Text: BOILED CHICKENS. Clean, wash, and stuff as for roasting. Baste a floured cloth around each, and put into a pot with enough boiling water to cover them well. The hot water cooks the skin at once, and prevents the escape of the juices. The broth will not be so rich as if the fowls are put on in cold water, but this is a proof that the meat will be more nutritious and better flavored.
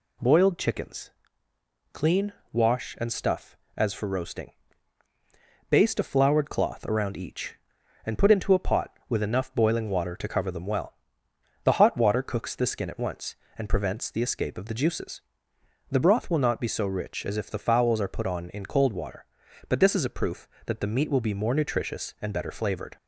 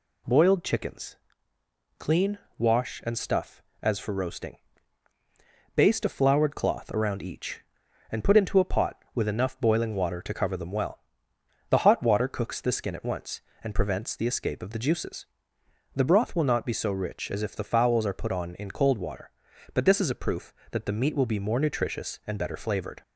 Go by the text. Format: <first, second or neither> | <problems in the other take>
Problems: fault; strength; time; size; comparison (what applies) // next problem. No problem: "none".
neither | none